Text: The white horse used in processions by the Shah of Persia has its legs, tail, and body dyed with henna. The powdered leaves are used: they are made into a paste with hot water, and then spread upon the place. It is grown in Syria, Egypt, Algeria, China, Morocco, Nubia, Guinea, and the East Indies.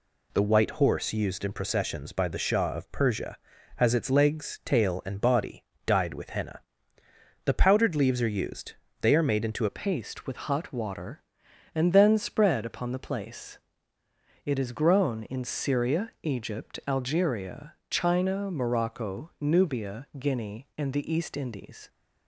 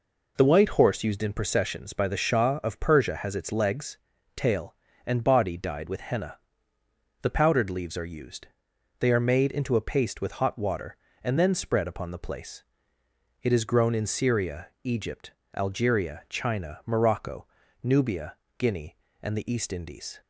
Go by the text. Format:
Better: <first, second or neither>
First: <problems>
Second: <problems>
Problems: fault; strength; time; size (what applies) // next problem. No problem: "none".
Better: second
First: pauses between "body" and "dyed"; slight; at 5.6 s; 0.22 s long // changes voice at "a"; from 9.6 s on; 12.2 s long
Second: none